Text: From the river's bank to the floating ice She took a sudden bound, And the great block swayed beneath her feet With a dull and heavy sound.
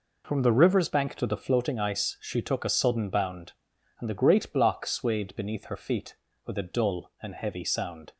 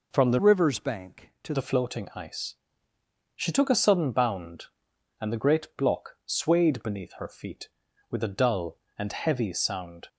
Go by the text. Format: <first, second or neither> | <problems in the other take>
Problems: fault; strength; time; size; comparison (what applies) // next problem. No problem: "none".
first | changes voice from "river's" to "to"; from 0.3 to 1.5 s; 1.2 s long // pauses between "ice" and "She"; noticeable; at 2.5 s; 0.80 s long